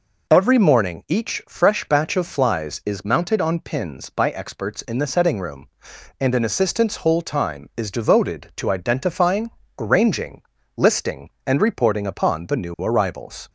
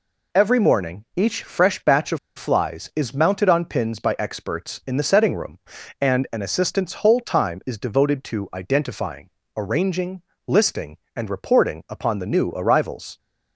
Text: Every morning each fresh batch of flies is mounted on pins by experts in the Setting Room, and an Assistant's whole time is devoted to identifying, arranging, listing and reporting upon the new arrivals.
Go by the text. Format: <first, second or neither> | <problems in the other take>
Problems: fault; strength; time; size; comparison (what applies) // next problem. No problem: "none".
first | pauses between "of" and "flies"; slight; at 2.1 s; 0.19 s long